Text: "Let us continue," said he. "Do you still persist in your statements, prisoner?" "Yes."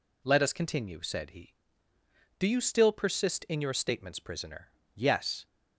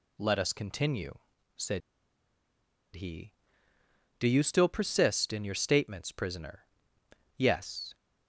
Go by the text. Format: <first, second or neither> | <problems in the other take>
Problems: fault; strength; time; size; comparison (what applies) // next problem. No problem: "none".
first | pauses between "said" and "he"; at 1.8 s; 1.1 s long